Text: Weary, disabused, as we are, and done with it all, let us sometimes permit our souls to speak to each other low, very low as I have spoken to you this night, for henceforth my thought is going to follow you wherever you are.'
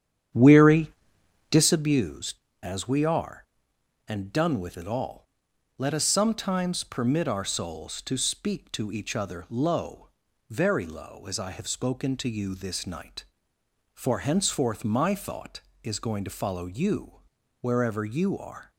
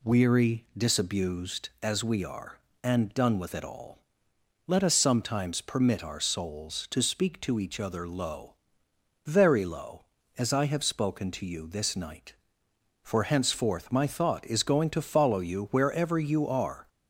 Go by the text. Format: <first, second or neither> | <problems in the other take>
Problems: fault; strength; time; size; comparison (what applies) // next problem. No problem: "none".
second | starts louder than the rest; strong; until 1.9 s; 9 dB // pauses between "you" and "wherever"; at 17.1 s; 0.42 s long